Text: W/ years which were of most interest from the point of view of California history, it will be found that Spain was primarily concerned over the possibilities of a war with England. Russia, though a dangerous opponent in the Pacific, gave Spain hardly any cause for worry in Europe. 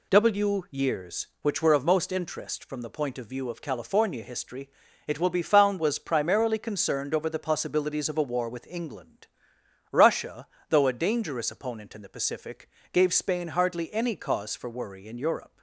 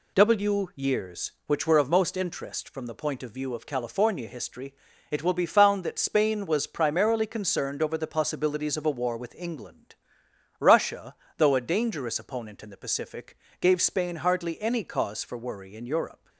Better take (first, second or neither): second